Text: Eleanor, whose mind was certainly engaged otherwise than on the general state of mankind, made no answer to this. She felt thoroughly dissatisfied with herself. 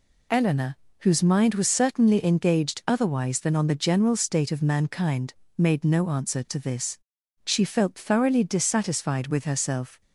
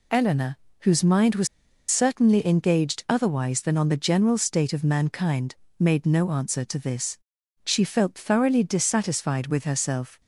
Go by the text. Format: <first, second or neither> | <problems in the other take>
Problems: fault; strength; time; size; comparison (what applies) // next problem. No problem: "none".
first | pauses between "was" and "certainly"; at 1.4 s; 0.42 s long